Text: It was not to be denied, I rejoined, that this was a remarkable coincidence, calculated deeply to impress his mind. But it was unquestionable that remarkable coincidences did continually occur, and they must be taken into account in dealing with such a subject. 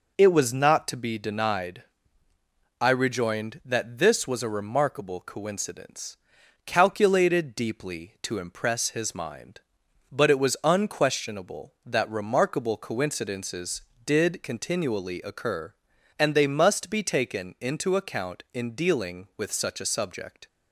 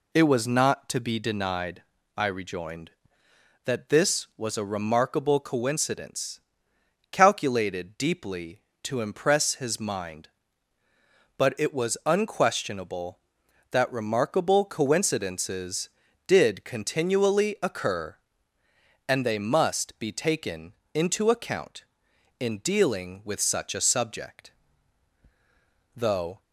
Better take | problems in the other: first | pauses between "taken" and "into"; slight; at 20.7 s; 0.18 s long // goes on to say "Though"; slight; from 25.9 s on; 0.46 s long

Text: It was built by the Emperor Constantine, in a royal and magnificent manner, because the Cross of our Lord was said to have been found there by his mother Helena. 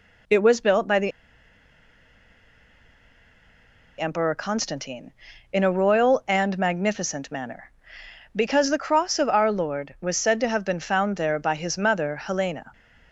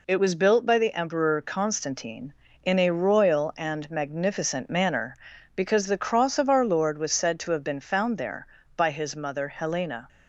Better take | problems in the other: second | pauses between "the" and "Emperor"; strong; at 1.1 s; 2.8 s long

